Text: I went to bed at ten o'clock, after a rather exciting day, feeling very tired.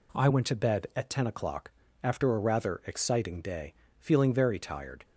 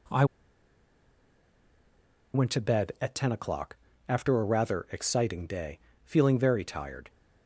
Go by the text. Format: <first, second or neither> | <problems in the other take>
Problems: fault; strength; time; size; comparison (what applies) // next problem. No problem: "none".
first | pauses between "I" and "went"; strong; at 0.2 s; 2.0 s long